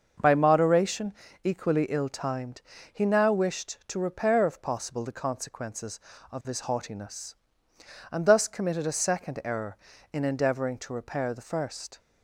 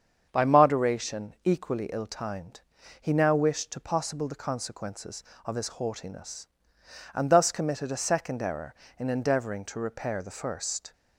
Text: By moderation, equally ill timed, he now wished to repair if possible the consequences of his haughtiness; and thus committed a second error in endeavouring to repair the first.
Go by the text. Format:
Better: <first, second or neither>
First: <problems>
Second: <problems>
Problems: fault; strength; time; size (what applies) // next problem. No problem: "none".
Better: first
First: starts louder than the rest; until 1.5 s; 6 dB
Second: starts louder than the rest; strong; until 1.3 s; 7.5 dB // skips "repair if"; at 3.8 s